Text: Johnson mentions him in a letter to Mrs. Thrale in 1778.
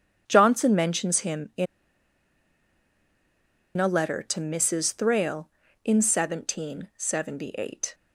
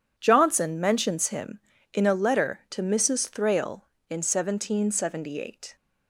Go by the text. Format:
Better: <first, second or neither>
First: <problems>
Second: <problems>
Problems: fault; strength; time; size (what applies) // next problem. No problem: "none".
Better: second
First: starts louder than the rest; strong; until 1.2 s; 8 dB // pauses between "in" and "a"; strong; at 1.6 s; 2.1 s long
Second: none